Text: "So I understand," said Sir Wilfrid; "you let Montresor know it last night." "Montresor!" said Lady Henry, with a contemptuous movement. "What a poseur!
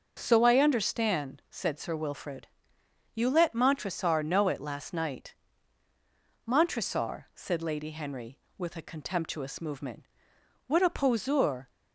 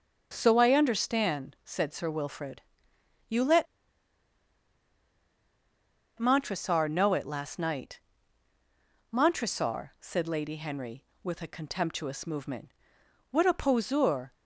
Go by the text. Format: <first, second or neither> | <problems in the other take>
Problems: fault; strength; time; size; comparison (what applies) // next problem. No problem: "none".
first | pauses between "let" and "Montresor"; strong; at 3.6 s; 2.5 s long